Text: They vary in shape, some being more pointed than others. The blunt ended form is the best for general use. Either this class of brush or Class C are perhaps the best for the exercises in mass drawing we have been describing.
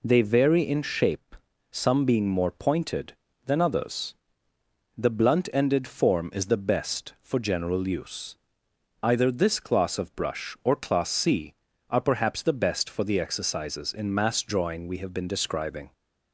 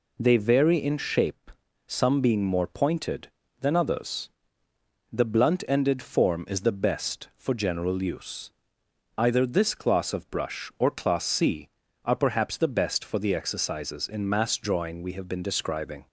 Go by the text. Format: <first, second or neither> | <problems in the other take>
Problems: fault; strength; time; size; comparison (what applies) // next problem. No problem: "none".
neither | none